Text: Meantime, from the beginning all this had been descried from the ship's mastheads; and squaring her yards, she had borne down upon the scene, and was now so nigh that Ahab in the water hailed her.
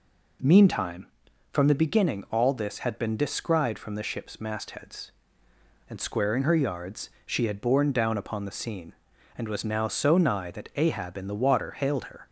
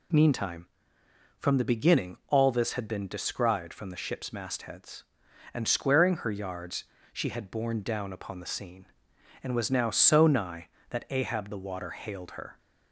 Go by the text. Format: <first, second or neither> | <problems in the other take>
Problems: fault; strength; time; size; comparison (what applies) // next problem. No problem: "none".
first | skips "in"; at 11.4 s